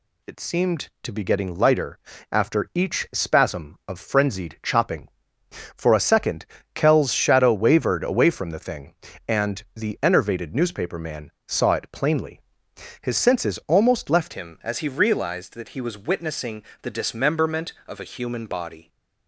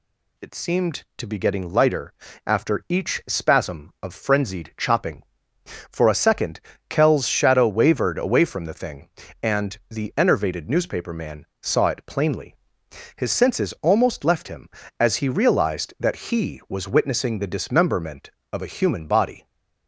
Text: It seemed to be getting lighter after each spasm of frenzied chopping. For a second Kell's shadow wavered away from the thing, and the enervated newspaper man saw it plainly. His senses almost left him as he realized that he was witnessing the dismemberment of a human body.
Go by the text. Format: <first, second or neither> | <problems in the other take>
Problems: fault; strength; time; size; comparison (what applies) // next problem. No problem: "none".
second | pauses between "lighter" and "after"; slight; at 1.9 s; 0.32 s long; slight in the second // pauses between "second" and "Kell's"; slight; at 6.4 s; 0.28 s long; slight in the second // pauses between "man" and "saw"; slight; at 11.3 s; 0.16 s long; slight in the second // changes voice at "him"; from 14.3 s on; 4.5 s long // pauses between "witnessing" and "the"; slight; at 16.6 s; 0.18 s long